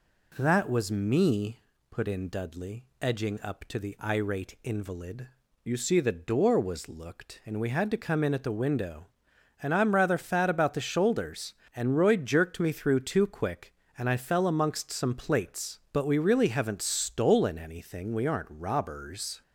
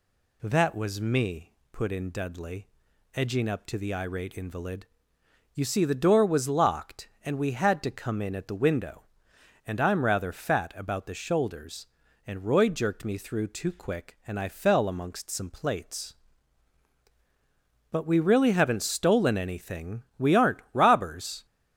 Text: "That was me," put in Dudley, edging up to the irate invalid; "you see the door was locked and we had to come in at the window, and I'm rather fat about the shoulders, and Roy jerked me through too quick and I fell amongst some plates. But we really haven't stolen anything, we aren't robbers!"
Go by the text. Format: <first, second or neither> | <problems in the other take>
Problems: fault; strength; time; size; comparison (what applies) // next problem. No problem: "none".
second | says "looked" for "locked"; at 6.8 s